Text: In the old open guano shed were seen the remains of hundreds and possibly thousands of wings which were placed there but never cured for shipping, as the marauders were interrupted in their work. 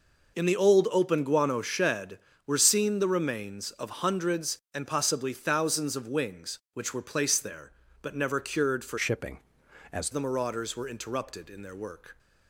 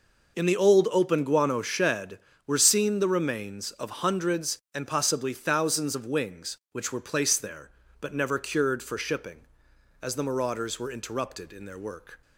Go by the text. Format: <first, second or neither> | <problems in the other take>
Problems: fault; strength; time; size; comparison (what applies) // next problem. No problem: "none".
second | changes voice from "shipping" to "as"; from 8.9 to 10.1 s; 1.2 s long